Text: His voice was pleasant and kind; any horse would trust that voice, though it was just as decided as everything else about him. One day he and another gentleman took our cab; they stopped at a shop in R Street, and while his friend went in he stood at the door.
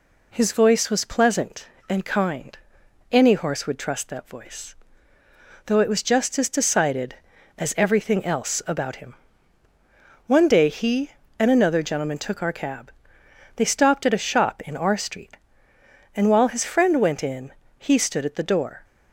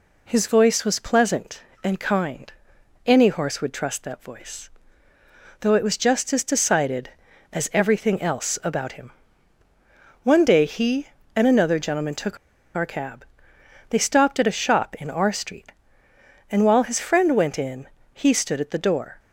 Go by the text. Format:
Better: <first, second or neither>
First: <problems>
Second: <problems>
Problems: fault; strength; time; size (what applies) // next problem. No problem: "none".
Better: first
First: pauses between "in" and "he"; slight; at 17.5 s; 0.24 s long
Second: pauses between "took" and "our"; at 12.3 s; 0.39 s long // pauses between "in" and "he"; slight; at 17.8 s; 0.24 s long